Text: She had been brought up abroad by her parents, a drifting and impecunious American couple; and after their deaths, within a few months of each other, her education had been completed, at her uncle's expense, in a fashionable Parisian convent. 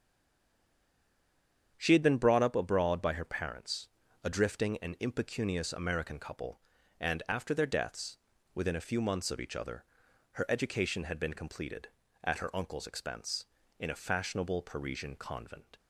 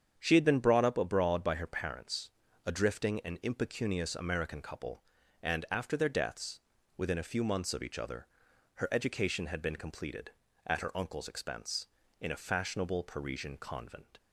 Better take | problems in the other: second | stays silent before the first word; noticeable; until 1.7 s; 1.7 s long // starts louder than the rest; strong; until 2.7 s; 8 dB; strong in the second

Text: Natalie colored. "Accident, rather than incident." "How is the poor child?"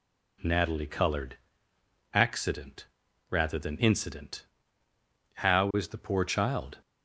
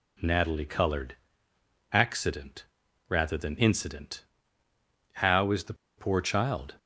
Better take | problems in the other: first | pauses between "the" and "poor"; slight; at 5.7 s; 0.23 s long

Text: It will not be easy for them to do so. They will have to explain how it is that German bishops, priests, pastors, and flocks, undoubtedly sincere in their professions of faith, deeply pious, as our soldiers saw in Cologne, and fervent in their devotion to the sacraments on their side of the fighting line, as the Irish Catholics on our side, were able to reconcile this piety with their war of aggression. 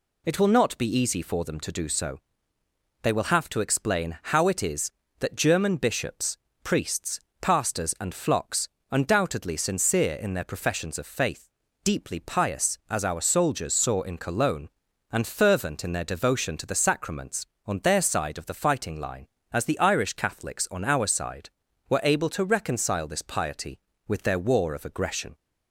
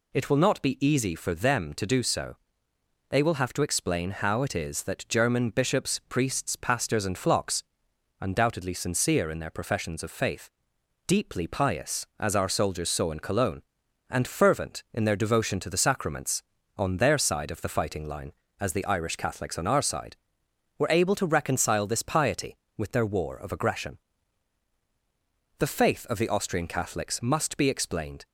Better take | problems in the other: first | goes on to say "The faith of the Austrian Catholics must be explained"; strong; from 25.5 s on; 2.6 s long

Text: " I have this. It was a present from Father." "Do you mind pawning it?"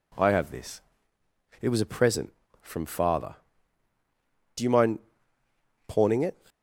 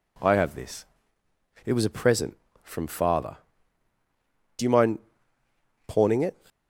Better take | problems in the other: neither | pauses between "mind" and "pawning"; noticeable; the same in both

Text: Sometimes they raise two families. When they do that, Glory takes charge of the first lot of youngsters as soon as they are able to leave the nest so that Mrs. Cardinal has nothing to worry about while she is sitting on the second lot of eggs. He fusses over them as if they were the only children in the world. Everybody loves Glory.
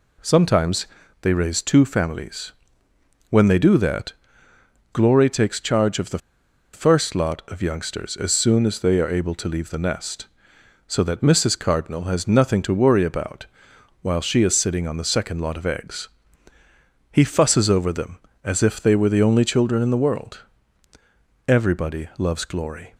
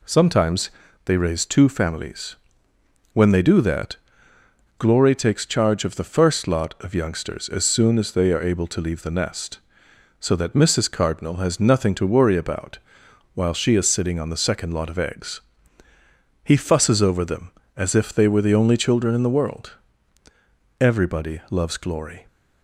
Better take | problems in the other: second | pauses between "Sometimes" and "they"; slight; at 0.8 s; 0.36 s long; slight in the second // pauses between "the" and "first"; noticeable; at 6.1 s; 0.55 s long // pauses between "about" and "while"; noticeable; at 13.4 s; 0.56 s long; noticeable in the second

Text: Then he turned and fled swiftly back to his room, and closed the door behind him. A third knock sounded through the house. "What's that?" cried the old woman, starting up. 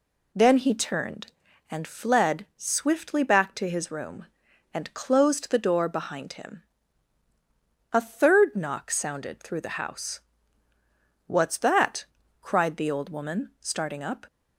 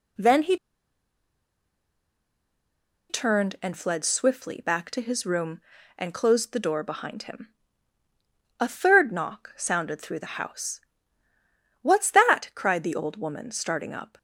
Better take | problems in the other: first | pauses between "he" and "turned"; strong; at 0.5 s; 2.5 s long

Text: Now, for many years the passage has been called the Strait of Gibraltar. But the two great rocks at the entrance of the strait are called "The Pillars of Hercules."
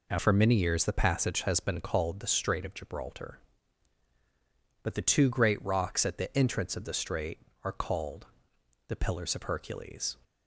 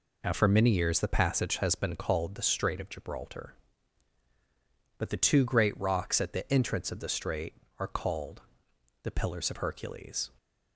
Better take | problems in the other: neither | pauses between "called" and "The"; noticeable; the same in both

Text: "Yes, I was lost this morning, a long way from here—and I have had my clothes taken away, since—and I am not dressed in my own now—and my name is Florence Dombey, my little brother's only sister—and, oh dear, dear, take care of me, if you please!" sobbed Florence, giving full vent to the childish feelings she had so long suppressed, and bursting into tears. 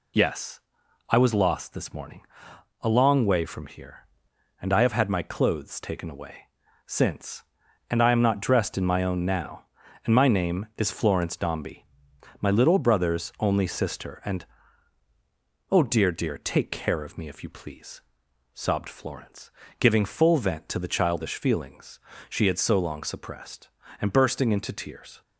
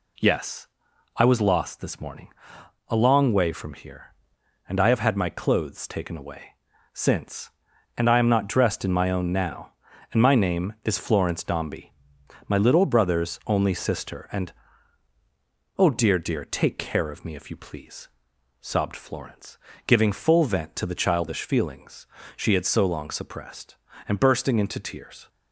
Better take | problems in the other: second | loses the start of "Yes"; at 0.1 s; 35 ms // pauses between "feelings" and "she"; slight; at 21.9 s; 0.28 s long; slight in the second

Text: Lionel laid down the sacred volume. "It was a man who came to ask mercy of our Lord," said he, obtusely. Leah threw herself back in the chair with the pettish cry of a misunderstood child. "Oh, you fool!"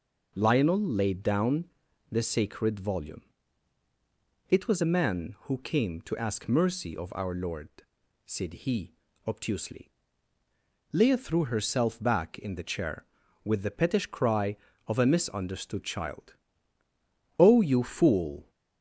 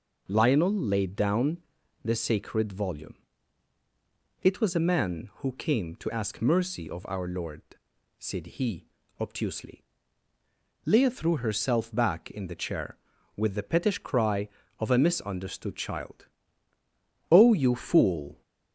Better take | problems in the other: neither | pauses between "down" and "the"; the same in both

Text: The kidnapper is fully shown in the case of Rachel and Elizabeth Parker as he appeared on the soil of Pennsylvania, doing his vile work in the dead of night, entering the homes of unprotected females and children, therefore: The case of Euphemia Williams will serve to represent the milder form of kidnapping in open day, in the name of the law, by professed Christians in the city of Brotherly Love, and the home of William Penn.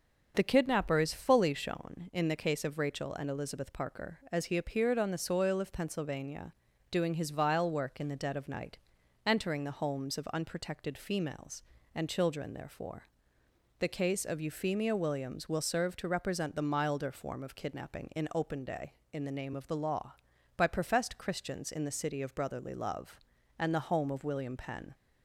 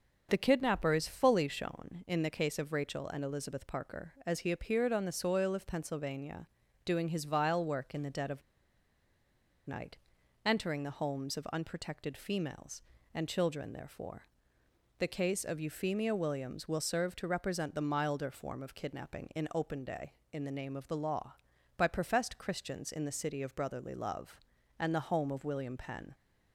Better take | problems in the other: first | starts louder than the rest; noticeable; until 1.3 s; 6 dB; noticeable in the first // pauses between "of" and "night"; strong; at 8.3 s; 1.2 s long

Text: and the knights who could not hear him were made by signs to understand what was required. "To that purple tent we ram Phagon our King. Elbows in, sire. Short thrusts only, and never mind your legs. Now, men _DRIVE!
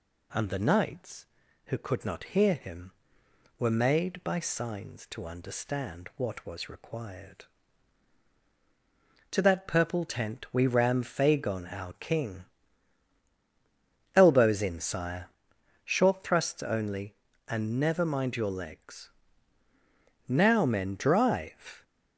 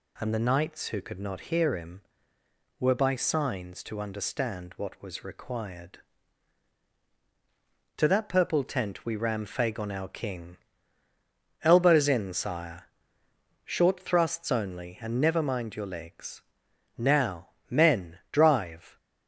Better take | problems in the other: first | skips "made"; at 2.9 s

